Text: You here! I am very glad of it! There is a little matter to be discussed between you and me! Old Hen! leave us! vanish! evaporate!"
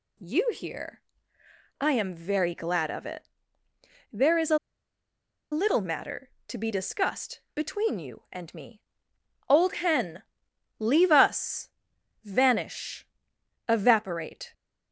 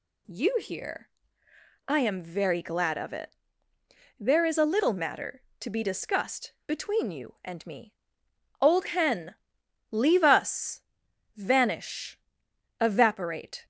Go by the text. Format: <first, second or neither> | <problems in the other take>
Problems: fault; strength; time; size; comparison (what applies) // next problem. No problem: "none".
second | pauses between "a" and "little"; noticeable; at 4.5 s; 0.94 s long